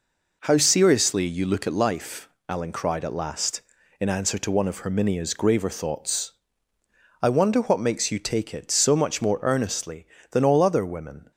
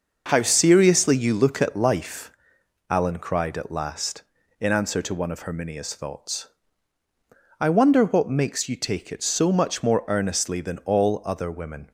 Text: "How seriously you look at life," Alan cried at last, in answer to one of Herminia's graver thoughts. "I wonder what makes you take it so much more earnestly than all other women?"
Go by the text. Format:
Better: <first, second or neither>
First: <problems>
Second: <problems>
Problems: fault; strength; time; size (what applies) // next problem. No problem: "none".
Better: first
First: none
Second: skips "graver"; at 5.9 s